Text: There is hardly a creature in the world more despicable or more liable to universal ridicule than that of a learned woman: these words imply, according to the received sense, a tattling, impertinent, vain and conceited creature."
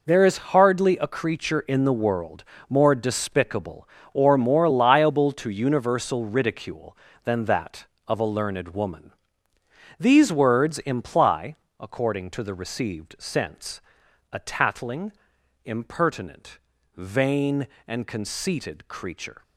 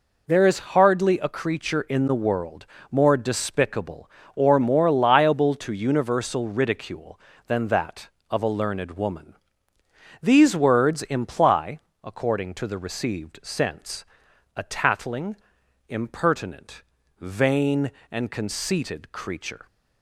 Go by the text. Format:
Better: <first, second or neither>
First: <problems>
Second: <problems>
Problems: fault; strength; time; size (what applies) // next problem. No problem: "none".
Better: second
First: gets quieter; strong; throughout; 11 dB // pauses between "world" and "more"; slight; at 2.4 s; 0.24 s long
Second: pauses between "world" and "more"; slight; at 2.6 s; 0.24 s long